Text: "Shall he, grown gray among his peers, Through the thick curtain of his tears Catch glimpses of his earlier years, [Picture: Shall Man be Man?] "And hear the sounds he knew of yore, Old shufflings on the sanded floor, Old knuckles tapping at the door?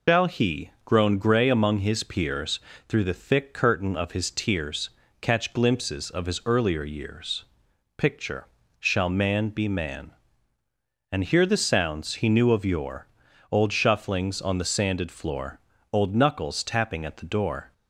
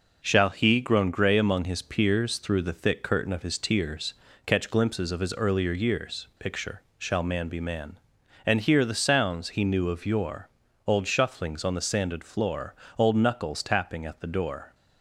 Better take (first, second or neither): second